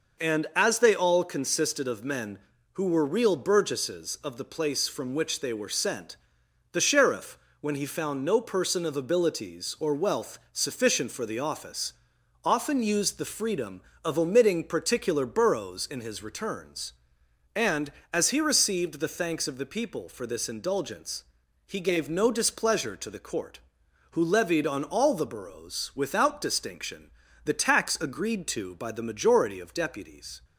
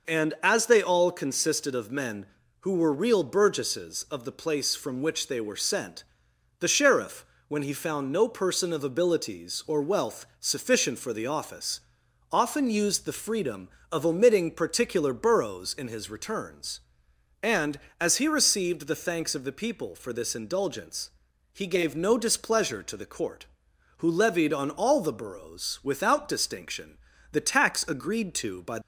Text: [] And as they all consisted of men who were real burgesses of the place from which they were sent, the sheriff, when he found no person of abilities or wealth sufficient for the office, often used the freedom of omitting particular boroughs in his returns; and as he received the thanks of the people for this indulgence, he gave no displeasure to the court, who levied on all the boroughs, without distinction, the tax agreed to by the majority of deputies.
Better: first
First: none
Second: stops before "the majority of deputies"; at 28.8 s

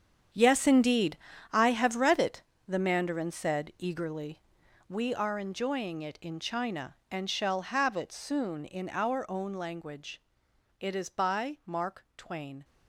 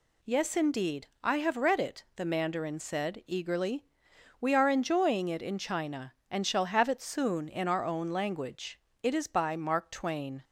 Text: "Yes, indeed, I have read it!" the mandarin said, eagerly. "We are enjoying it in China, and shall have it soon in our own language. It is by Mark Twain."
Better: second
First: gets quieter; strong; throughout; 12 dB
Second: none

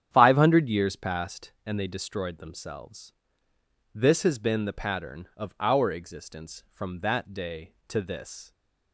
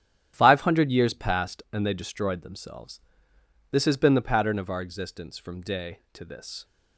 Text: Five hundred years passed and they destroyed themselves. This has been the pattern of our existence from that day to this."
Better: first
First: starts louder than the rest; strong; until 1.1 s; 9 dB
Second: starts louder than the rest; strong; until 1.3 s; 11 dB // skips "that"; at 5.6 s

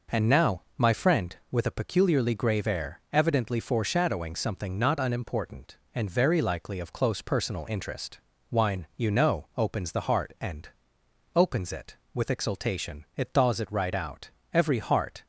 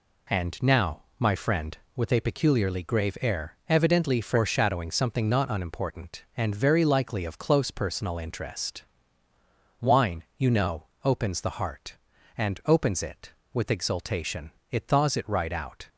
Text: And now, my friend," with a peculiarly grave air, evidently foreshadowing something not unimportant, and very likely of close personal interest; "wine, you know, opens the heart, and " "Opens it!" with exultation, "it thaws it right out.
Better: second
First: goes on to say "Every heart"; noticeable; from 14.5 s on; 0.74 s long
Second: none

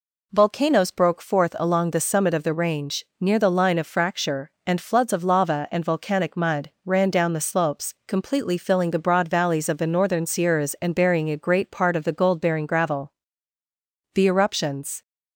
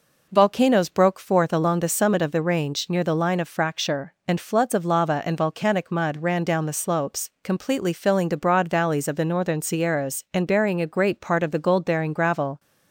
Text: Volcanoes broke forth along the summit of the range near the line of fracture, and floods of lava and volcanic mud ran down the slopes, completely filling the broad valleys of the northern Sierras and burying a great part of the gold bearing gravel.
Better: second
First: pauses between "range" and "near"; slight; at 3.0 s; 0.16 s long // pauses between "mud" and "ran"; slight; at 6.6 s; 0.16 s long // goes on to say "The eruptions"; noticeable; from 14.1 s on; 0.88 s long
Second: none

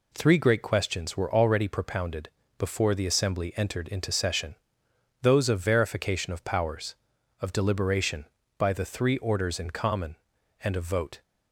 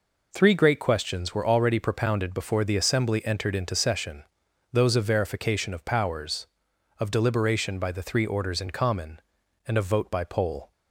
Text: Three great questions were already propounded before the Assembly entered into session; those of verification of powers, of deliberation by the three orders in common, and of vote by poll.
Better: second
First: pauses between "propounded" and "before"; slight; at 2.2 s; 0.28 s long // stops before "by poll"; at 11.2 s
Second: none

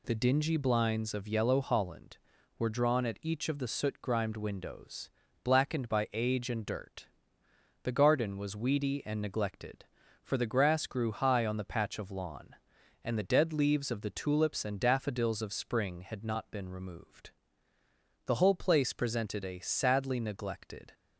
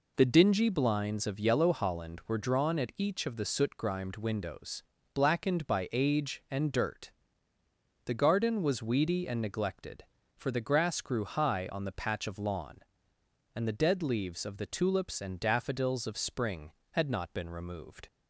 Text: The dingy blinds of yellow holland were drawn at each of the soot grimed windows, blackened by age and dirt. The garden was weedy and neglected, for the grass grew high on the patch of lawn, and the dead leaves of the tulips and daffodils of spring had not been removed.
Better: second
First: goes on to say "The whole place presented a sadly neglected"; strong; from 18.2 s on; 2.6 s long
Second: none

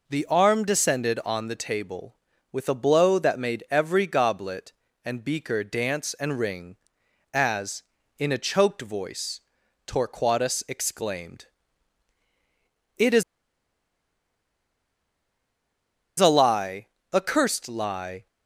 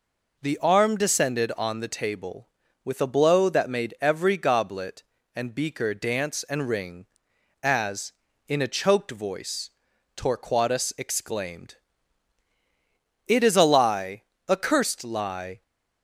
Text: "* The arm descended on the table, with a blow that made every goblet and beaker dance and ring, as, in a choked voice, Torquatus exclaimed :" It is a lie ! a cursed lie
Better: second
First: pauses between "is" and "a"; strong; at 13.2 s; 2.9 s long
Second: none

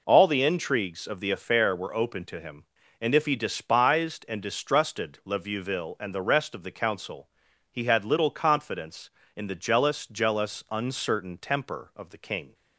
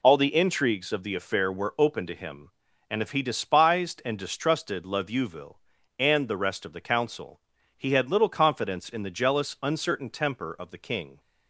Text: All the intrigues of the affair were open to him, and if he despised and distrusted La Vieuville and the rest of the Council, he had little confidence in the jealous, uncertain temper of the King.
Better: second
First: says "jealous" twice; at 10.0 s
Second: none

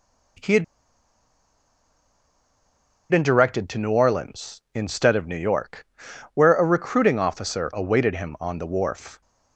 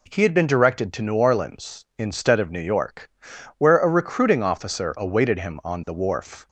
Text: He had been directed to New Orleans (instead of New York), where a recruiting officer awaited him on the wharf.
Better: second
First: pauses between "had" and "been"; strong; at 0.6 s; 2.4 s long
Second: none

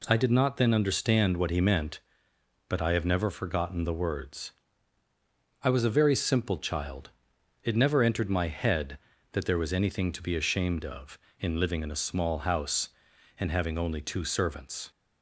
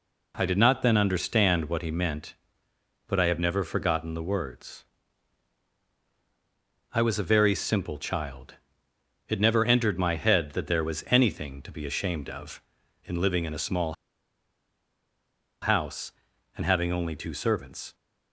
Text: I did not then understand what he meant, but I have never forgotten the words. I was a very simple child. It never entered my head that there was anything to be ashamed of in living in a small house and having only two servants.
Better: first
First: none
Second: pauses between "small" and "house"; strong; at 13.9 s; 1.6 s long

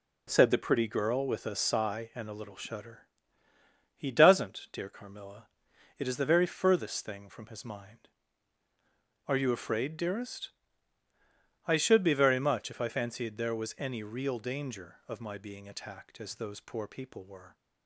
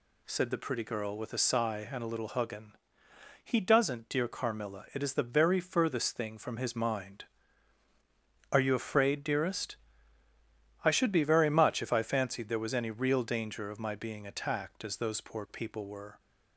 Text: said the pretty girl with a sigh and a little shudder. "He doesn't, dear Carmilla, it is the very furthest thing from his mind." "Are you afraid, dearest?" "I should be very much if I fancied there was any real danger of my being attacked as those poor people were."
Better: first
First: none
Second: says "huggin" for "shudder"; at 2.3 s

